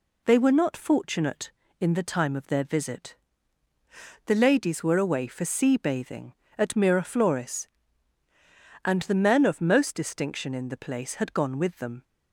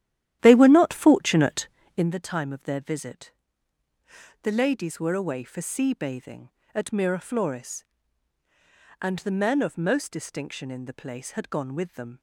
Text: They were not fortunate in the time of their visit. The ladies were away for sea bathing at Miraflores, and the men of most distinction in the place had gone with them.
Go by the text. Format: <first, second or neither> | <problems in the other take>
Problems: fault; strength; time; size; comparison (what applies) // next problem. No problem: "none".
first | starts louder than the rest; strong; until 2.1 s; 12 dB